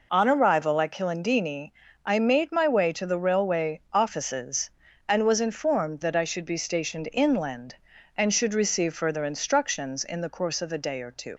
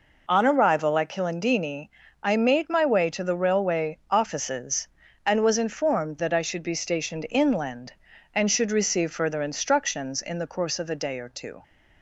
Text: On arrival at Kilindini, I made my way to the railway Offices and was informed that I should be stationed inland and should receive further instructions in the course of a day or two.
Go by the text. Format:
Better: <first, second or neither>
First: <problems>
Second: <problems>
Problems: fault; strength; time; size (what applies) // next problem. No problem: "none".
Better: second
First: leaves "two" unfinished; at 11.3 s; 80 ms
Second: none